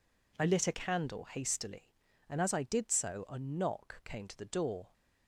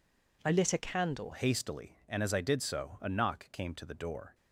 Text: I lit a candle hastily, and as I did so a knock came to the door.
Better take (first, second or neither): first